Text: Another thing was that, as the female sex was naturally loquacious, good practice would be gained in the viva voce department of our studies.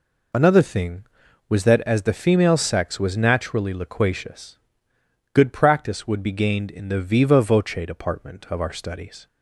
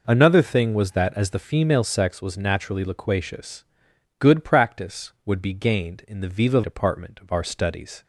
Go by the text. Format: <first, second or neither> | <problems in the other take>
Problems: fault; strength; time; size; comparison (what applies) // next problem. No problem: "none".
first | skips "voce"; at 6.6 s